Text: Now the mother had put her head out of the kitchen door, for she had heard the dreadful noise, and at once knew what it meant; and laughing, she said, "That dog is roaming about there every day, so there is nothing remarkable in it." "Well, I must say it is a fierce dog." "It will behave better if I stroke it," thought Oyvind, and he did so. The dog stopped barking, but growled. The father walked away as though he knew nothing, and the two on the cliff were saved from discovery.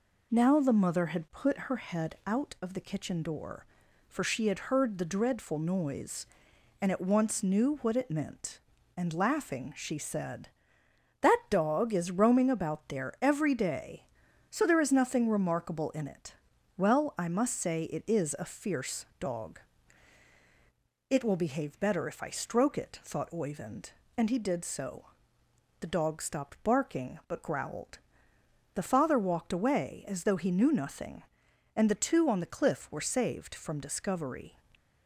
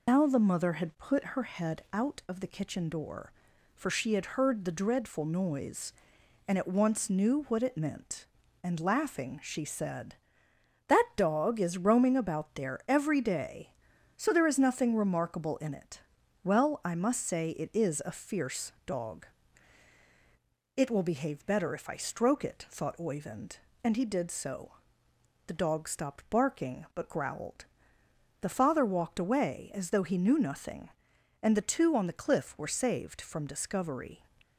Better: first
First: none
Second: loses the start of "Now"; at 0.0 s; 100 ms

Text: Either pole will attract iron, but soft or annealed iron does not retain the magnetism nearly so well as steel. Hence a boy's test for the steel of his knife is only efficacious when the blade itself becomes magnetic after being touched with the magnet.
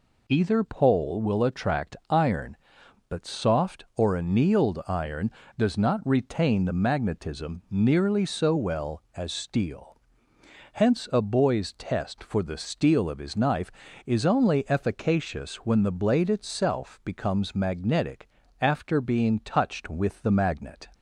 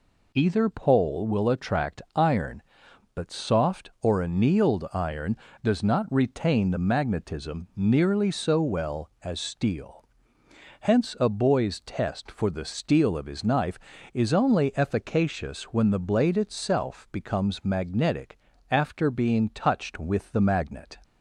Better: neither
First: pauses between "magnetic" and "after"; slight; at 18.2 s; 0.32 s long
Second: pauses between "magnetic" and "after"; slight; at 18.3 s; 0.32 s long

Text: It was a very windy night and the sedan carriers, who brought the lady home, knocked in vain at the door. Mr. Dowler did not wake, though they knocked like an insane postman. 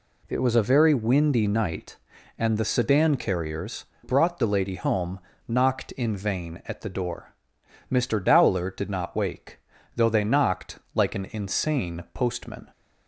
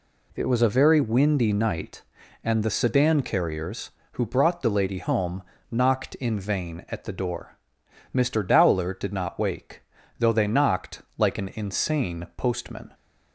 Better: second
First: skips "who"; at 3.9 s // pauses between "knocked" and "like"; slight; at 10.7 s; 0.16 s long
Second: pauses between "knocked" and "like"; slight; at 11.0 s; 0.16 s long

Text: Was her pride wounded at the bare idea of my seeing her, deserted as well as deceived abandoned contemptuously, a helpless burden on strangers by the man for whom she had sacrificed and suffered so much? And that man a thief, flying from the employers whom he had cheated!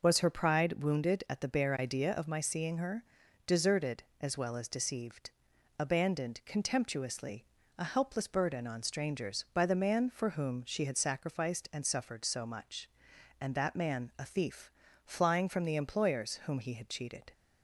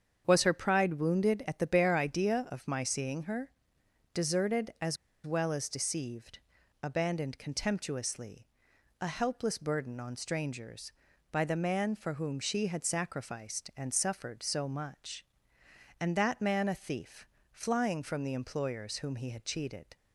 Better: first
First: pauses between "deceived" and "abandoned"; noticeable; at 5.2 s; 0.50 s long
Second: starts louder than the rest; strong; until 1.2 s; 7.5 dB // pauses between "as" and "well"; slight; at 4.9 s; 0.28 s long // pauses between "deceived" and "abandoned"; noticeable; at 6.3 s; 0.46 s long

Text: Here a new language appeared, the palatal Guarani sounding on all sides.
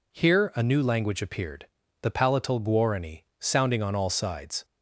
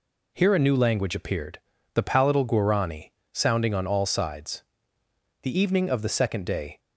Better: first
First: none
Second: pauses between "Guarani" and "sounding"; slight; at 3.1 s; 0.20 s long // goes on to say "The evening of the second day"; from 5.4 s on; 1.3 s long

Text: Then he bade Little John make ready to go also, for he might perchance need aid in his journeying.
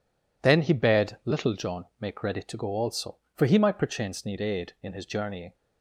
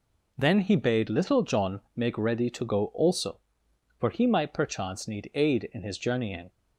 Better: neither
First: none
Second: none

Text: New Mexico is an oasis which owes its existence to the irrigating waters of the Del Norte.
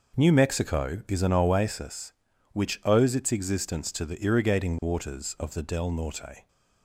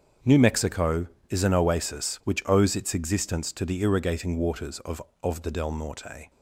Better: first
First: none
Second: starts louder than the rest; strong; until 1.4 s; 7 dB // says "of" twice; at 5.2 s

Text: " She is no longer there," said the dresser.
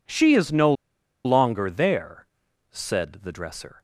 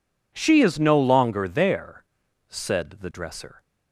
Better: second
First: pauses between "no" and "longer"; noticeable; at 0.7 s; 0.52 s long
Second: none

